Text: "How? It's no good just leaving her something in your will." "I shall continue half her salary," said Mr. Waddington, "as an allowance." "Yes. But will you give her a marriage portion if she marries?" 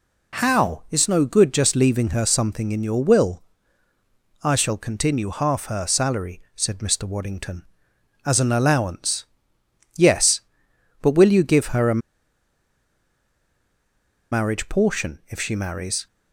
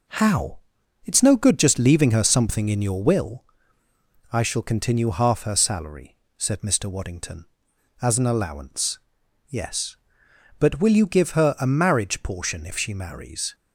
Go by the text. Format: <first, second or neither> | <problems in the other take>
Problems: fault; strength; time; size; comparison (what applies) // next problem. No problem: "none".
second | pauses between "a" and "marriage"; strong; at 11.9 s; 2.3 s long